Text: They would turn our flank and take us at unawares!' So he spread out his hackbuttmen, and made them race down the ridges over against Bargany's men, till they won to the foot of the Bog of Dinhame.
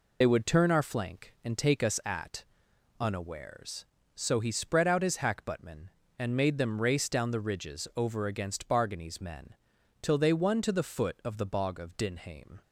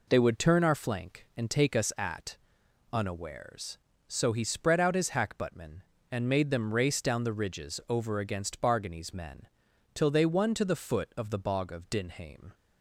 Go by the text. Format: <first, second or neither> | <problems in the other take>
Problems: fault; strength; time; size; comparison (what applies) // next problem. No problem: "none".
second | loses the start of "They"; at 0.2 s; 45 ms // pauses between "at" and "unawares"; noticeable; at 2.4 s; 0.54 s long; noticeable in the second